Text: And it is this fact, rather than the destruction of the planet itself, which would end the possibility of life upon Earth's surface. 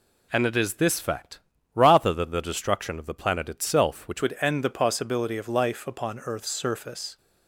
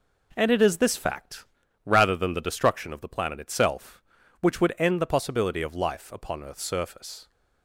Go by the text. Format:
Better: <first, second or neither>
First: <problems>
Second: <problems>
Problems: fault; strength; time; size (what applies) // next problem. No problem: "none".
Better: second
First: changes voice at "would"; from 4.2 s on; 2.9 s long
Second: none